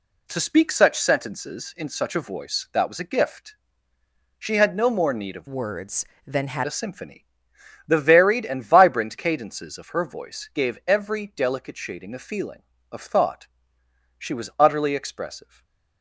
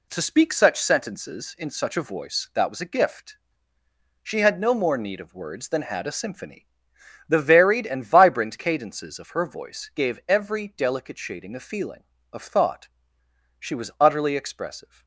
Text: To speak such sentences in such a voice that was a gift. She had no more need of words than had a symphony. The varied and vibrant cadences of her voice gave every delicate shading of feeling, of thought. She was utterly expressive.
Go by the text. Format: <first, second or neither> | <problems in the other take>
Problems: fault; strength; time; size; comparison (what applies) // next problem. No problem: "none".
second | changes voice from "words" to "had"; from 5.4 to 6.6 s; 1.2 s long // stays silent after the last word; slight; from 15.4 s on; 0.6 s long